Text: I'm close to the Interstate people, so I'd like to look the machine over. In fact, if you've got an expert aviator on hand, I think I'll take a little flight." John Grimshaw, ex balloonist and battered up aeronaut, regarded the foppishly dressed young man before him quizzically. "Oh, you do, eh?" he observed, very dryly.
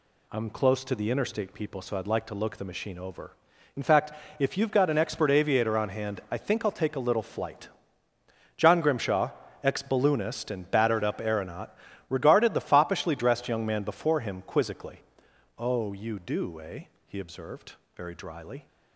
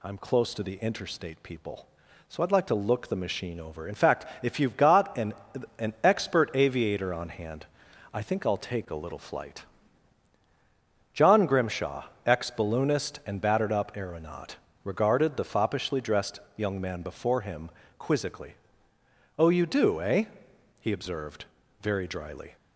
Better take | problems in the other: first | says "an" twice; at 5.7 s // pauses between "dressed" and "young"; slight; at 16.3 s; 0.18 s long // pauses between "him" and "quizzically"; slight; at 17.6 s; 0.28 s long

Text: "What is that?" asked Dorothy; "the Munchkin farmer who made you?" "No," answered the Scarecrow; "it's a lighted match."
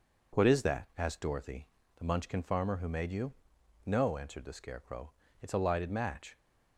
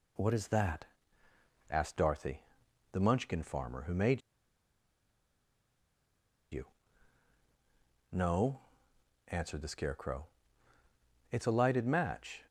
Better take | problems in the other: first | pauses between "made" and "you"; strong; at 4.2 s; 2.3 s long

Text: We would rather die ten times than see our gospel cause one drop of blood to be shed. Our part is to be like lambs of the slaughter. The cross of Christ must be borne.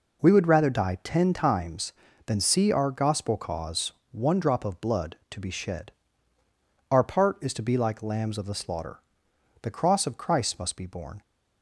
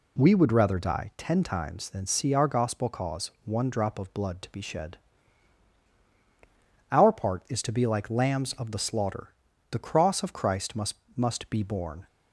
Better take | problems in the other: first | pauses between "cause" and "one"; slight; at 3.2 s; 0.16 s long; slight in the first // says "must" twice; at 11.1 s

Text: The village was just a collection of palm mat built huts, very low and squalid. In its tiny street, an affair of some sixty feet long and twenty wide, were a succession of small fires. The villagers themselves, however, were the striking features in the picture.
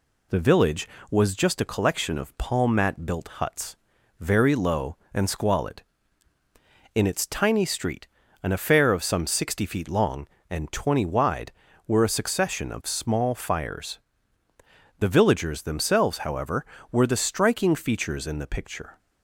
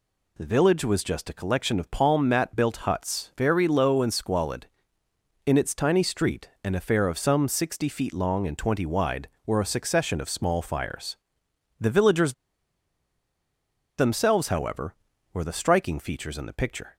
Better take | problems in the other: first | pauses between "villagers" and "themselves"; strong; at 12.3 s; 1.6 s long

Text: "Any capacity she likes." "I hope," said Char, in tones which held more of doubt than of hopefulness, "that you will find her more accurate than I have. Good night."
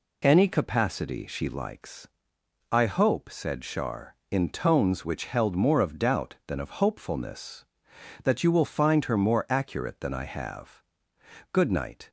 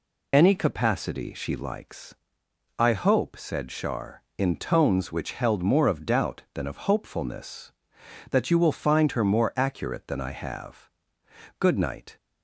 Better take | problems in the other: first | loses the start of "Any"; at 0.3 s; 40 ms

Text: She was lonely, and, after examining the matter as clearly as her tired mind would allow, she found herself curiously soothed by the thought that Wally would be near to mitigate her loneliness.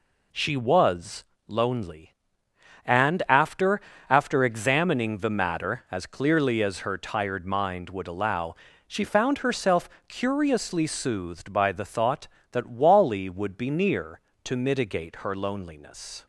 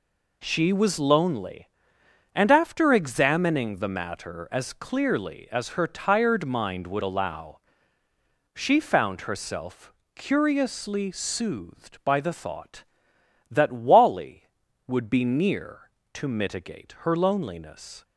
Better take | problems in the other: second | pauses between "was" and "lonely"; slight; at 1.2 s; 0.22 s long // says "after" twice; at 4.0 s // pauses between "herself" and "curiously"; slight; at 9.8 s; 0.18 s long; slight in the second

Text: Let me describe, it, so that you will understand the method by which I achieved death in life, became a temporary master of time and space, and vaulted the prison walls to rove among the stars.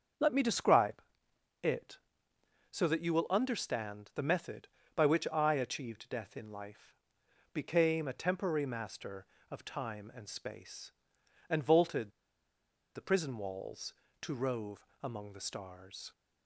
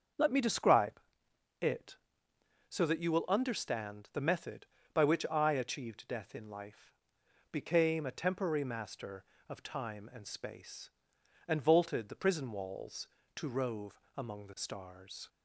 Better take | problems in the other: second | starts louder than the rest; until 1.7 s; 7 dB; also in the second // pauses between "vaulted" and "the"; noticeable; at 12.1 s; 0.84 s long // pauses between "rove" and "among"; slight; at 14.8 s; 0.16 s long; slight in the second

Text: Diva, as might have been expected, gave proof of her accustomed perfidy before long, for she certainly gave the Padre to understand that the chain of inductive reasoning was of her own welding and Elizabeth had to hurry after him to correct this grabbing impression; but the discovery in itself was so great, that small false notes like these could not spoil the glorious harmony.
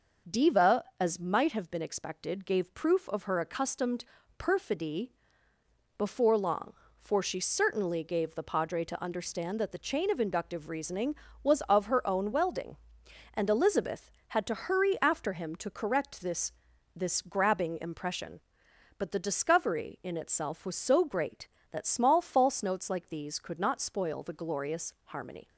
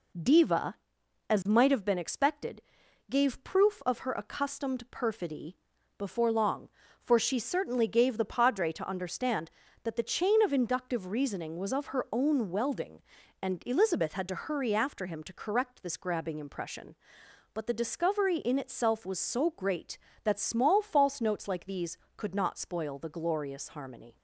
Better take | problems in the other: second | starts louder than the rest; until 1.4 s; 6 dB // pauses between "accustomed" and "perfidy"; slight; at 4.0 s; 0.34 s long // pauses between "perfidy" and "before"; noticeable; at 5.1 s; 0.86 s long; also in the second // says "this" twice; at 16.9 s

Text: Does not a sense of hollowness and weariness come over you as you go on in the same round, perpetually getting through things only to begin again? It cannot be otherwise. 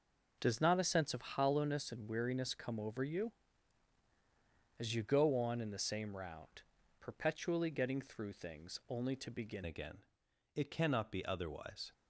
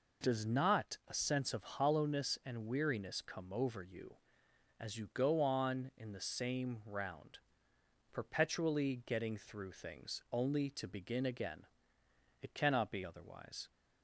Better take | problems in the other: second | changes voice at "again"; from 9.6 s on; 2.3 s long

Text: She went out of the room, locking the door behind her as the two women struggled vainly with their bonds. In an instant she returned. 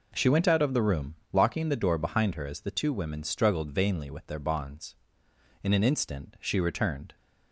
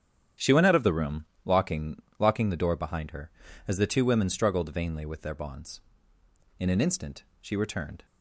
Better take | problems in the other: first | starts louder than the rest; strong; until 1.5 s; 9 dB // says "locking" twice; at 2.1 s // pauses between "instant" and "she"; slight; at 7.2 s; 0.16 s long

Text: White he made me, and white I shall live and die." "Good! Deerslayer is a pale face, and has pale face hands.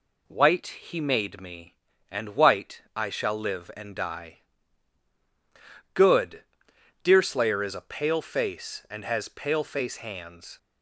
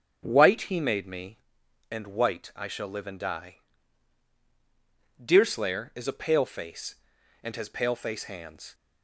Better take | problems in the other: first | starts louder than the rest; strong; until 1.2 s; 8.5 dB // skips "Good"; at 4.3 s

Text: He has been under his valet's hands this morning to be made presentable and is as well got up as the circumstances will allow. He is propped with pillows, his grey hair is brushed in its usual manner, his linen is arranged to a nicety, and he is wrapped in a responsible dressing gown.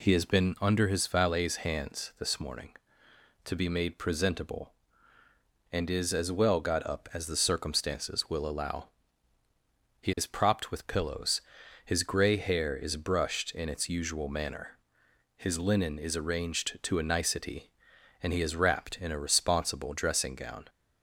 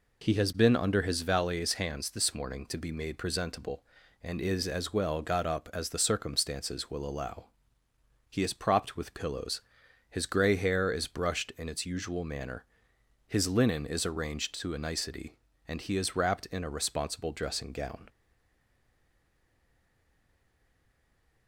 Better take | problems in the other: first | stays silent after the last word; strong; from 18.0 s on; 3.4 s long

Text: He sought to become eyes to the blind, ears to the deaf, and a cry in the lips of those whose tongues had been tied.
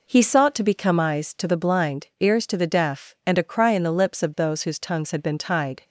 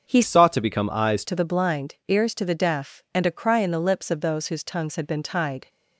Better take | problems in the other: first | starts louder than the rest; until 1.1 s; 6.5 dB // changes voice from "sought" to "eyes"; from 0.2 to 1.2 s; 1.0 s long

